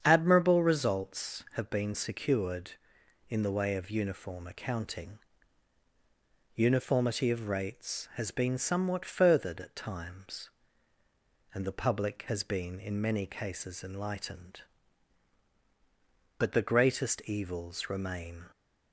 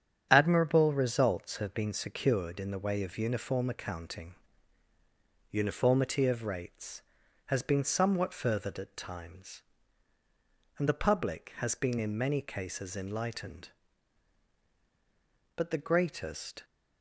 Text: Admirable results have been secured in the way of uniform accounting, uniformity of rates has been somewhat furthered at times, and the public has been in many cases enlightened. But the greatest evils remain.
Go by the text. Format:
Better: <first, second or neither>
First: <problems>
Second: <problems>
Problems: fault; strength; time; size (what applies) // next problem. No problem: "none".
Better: first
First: starts louder than the rest; strong; until 1.0 s; 8 dB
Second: starts louder than the rest; strong; until 1.3 s; 9 dB // stops before "evils remain"; at 16.6 s